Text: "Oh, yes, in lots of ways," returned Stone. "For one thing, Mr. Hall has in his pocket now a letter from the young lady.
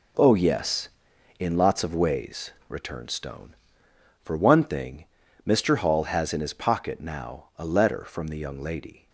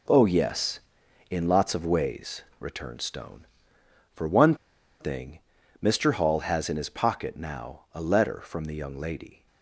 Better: first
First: none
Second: pauses between "one" and "thing"; at 4.5 s; 0.45 s long

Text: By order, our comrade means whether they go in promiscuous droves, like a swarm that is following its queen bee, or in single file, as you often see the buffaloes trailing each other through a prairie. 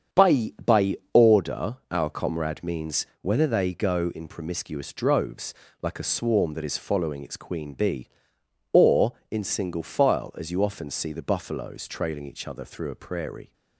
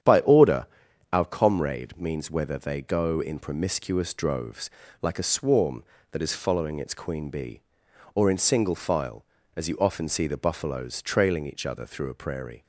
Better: second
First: starts louder than the rest; strong; until 1.4 s; 8 dB // says "By" twice; at 0.6 s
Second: starts louder than the rest; strong; until 1.5 s; 9 dB

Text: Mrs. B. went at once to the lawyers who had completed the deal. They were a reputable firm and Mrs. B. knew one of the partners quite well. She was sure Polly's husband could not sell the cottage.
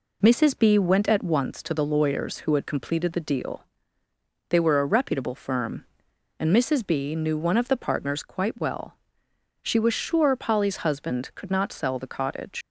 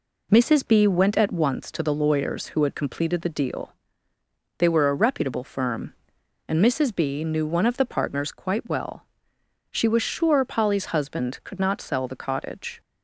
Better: second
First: leaves "cottage" unfinished; at 12.6 s; 100 ms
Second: none

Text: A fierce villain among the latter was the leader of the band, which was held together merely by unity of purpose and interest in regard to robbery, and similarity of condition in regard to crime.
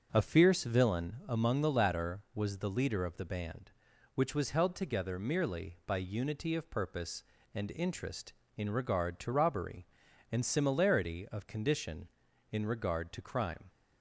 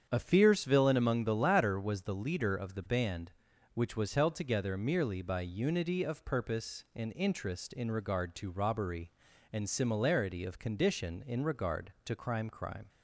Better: first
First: none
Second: starts louder than the rest; strong; until 1.1 s; 7.5 dB // says "crime" twice; at 12.4 s

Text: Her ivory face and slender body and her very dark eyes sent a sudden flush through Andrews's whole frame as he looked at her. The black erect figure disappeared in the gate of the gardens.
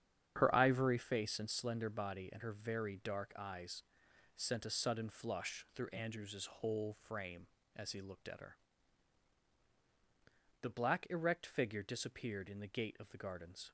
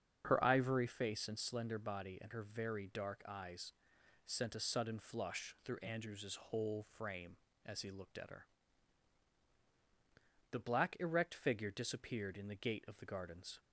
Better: second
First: gets quieter; strong; throughout; 10 dB // starts louder than the rest; strong; until 1.3 s; 8.5 dB // pauses between "eyes" and "sent"; noticeable; at 3.8 s; 0.52 s long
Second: starts louder than the rest; until 1.2 s; 7 dB // pauses between "eyes" and "sent"; noticeable; at 3.7 s; 0.52 s long

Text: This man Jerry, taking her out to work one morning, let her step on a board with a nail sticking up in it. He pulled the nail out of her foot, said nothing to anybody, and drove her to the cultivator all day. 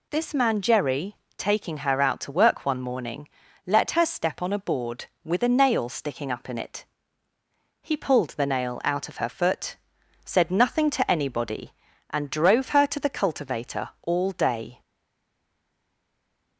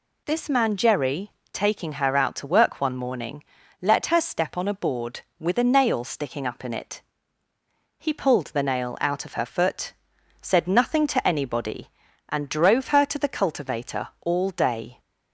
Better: second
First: stays silent after the last word; noticeable; from 14.8 s on; 1.7 s long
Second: none

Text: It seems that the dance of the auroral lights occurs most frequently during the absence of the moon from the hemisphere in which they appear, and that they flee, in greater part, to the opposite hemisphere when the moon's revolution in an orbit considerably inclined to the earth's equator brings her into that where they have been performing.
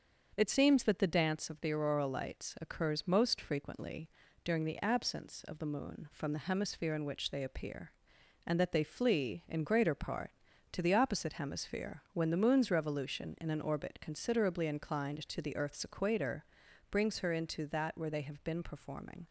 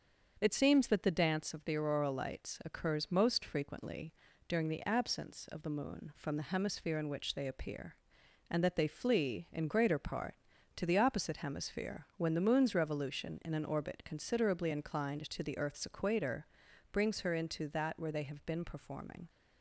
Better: neither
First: starts louder than the rest; until 1.3 s; 6.5 dB // pauses between "frequently" and "during"; slight; at 4.0 s; 0.36 s long // pauses between "equator" and "brings"; noticeable; at 16.4 s; 0.46 s long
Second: starts louder than the rest; until 1.4 s; 6.5 dB // pauses between "frequently" and "during"; slight; at 4.1 s; 0.36 s long // pauses between "equator" and "brings"; noticeable; at 16.4 s; 0.46 s long

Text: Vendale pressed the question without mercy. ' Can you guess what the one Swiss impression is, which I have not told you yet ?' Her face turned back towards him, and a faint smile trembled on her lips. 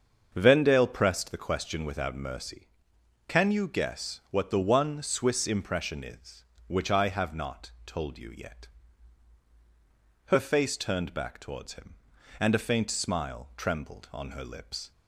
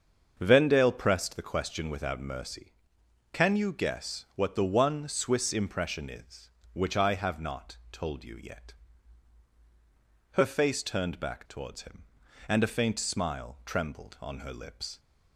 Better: neither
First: starts louder than the rest; strong; until 1.3 s; 8 dB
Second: starts louder than the rest; strong; until 1.3 s; 8 dB

